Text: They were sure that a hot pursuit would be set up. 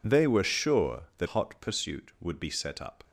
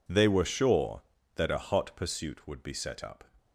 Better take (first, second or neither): second